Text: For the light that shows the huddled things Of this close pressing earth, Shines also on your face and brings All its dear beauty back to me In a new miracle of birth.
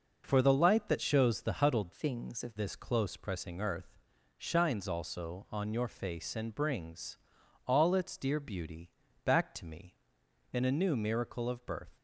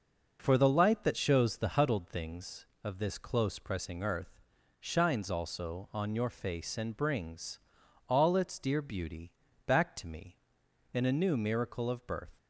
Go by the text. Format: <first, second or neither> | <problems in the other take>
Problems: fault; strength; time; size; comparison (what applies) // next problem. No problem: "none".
second | changes voice from "things" to "Of"; from 1.9 to 2.5 s; 0.6 s long // pauses between "brings" and "All"; noticeable; at 7.1 s; 0.50 s long; noticeable in the second // pauses between "beauty" and "back"; slight; at 8.9 s; 0.34 s long; slight in the second